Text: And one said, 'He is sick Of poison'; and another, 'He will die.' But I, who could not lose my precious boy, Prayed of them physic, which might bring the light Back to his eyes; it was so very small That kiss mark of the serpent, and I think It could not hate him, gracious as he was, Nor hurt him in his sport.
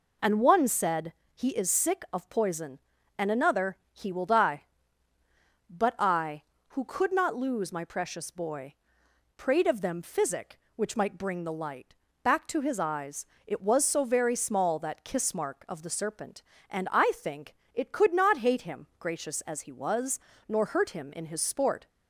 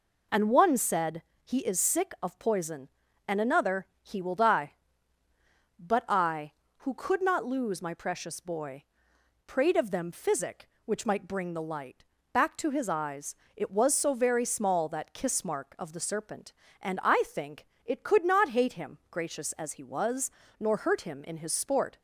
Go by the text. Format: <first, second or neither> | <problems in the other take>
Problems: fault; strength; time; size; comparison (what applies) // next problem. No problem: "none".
neither | pauses between "light" and "Back"; slight; the same in both // pauses between "think" and "It"; slight; the same in both